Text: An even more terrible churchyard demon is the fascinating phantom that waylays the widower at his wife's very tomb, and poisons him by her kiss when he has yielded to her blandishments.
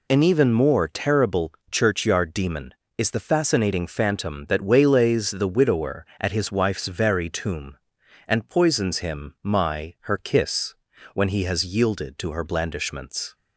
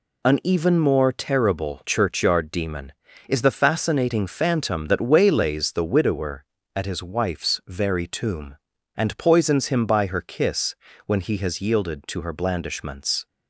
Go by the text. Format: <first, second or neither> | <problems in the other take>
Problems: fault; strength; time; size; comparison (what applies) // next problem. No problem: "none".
second | pauses between "terrible" and "churchyard"; slight; at 1.5 s; 0.18 s long // says "my" for "by"; at 9.4 s // pauses between "kiss" and "when"; at 10.7 s; 0.38 s long; slight in the second